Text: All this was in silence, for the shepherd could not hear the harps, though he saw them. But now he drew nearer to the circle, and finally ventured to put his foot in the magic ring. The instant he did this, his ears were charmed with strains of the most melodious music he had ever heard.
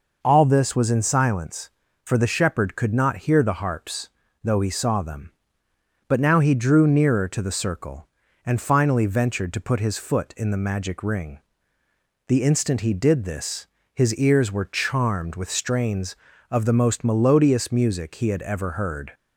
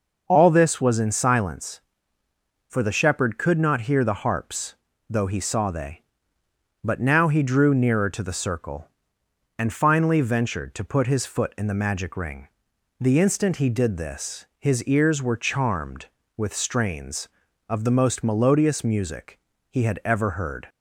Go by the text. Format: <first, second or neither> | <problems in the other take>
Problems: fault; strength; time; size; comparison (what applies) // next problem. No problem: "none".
first | says "they" for "them"; at 5.7 s // pauses between "music" and "he"; slight; at 19.3 s; 0.32 s long